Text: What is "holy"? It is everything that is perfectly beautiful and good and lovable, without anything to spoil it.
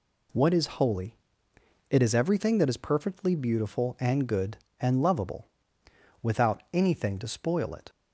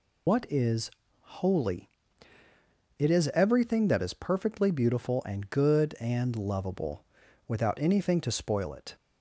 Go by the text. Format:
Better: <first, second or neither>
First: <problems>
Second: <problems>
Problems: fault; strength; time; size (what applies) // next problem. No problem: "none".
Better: first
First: none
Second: loses the start of "What"; at 0.2 s; 100 ms // pauses between "is" and "holy"; slight; at 0.9 s; 0.28 s long